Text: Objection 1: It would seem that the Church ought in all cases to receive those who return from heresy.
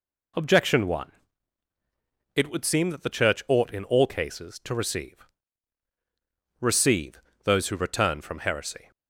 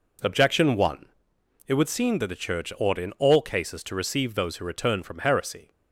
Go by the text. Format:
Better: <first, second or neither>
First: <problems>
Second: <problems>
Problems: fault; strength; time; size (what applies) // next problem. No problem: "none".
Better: second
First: says "receive" twice; at 6.6 s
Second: none